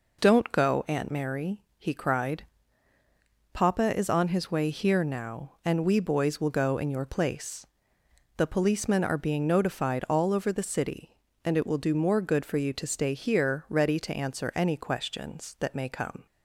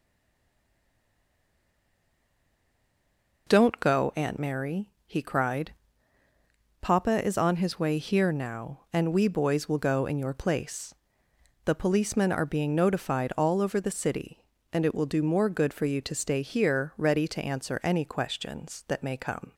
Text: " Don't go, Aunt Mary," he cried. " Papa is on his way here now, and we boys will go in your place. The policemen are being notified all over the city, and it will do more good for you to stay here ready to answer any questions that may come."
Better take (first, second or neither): first